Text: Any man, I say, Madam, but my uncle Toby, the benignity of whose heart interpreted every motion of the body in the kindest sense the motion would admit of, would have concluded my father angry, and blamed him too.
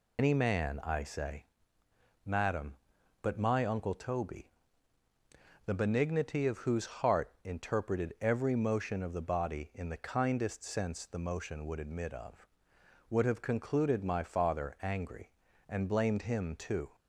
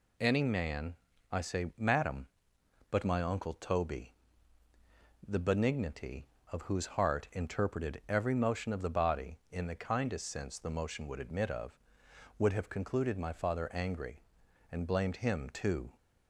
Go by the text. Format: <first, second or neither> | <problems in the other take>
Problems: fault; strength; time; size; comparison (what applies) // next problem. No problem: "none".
second | loses the start of "Any"; at 0.1 s; 100 ms